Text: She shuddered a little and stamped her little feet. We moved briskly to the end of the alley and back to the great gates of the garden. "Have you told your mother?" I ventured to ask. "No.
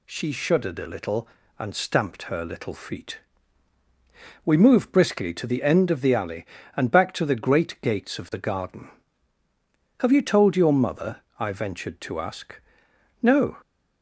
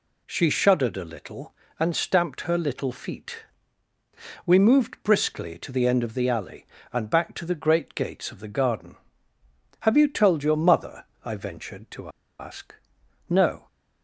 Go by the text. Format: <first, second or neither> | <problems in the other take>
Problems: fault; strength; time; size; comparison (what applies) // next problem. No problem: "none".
first | pauses between "to" and "ask"; slight; at 12.0 s; 0.30 s long